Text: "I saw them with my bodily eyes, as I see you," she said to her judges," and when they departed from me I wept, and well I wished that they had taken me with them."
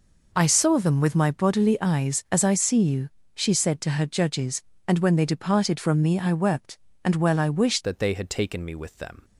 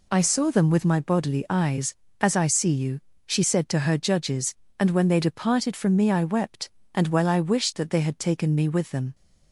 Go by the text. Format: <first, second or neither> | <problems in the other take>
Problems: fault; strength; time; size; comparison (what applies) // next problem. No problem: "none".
second | changes voice at "that"; from 7.8 s on; 1.4 s long